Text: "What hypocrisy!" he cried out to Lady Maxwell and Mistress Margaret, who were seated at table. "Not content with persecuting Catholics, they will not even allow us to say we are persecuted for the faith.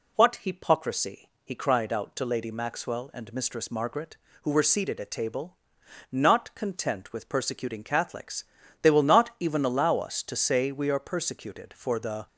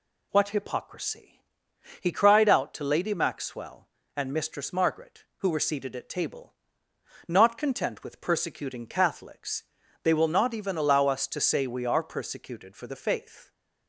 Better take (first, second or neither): second